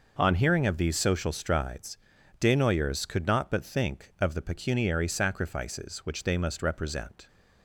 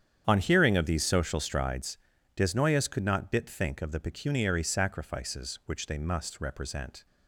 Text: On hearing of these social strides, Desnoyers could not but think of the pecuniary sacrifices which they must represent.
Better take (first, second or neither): first